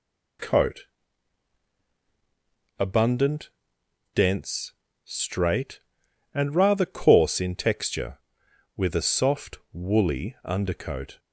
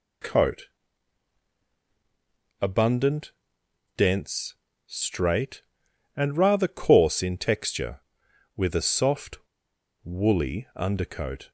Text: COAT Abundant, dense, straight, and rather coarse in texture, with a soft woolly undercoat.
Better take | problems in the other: first | pauses between "COAT" and "Abundant"; strong; at 0.6 s; 1.9 s long; strong in the first // pauses between "soft" and "woolly"; noticeable; at 9.3 s; 0.65 s long

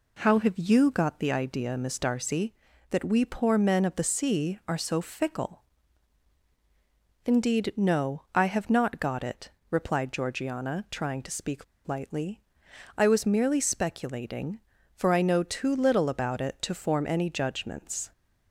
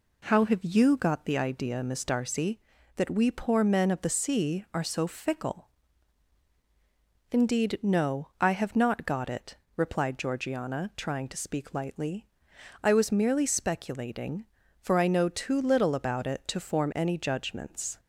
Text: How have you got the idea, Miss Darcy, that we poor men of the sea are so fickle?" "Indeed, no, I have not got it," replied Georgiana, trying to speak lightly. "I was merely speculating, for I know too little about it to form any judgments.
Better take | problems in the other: second | pauses between "speak" and "lightly"; slight; at 11.6 s; 0.22 s long

